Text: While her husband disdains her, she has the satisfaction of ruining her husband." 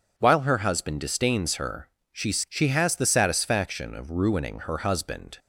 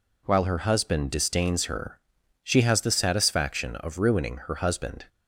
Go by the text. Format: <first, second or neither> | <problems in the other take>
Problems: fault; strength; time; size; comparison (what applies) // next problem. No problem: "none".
second | says "she" twice; at 2.3 s